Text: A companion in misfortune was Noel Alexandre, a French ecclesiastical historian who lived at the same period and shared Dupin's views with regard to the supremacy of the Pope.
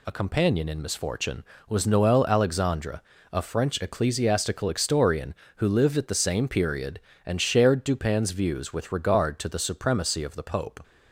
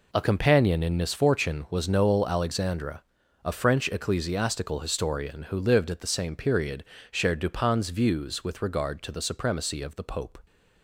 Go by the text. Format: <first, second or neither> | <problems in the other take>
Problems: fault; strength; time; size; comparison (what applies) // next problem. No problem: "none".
first | skips "and"; at 6.9 s